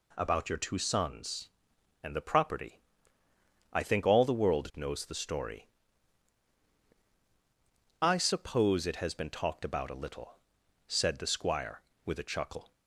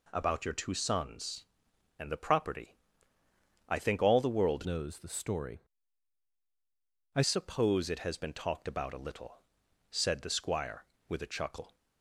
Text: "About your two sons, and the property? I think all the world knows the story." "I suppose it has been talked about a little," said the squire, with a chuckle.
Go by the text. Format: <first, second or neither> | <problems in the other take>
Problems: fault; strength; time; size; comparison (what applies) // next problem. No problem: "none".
first | changes voice from "knows" to "I"; from 4.6 to 7.2 s; 2.6 s long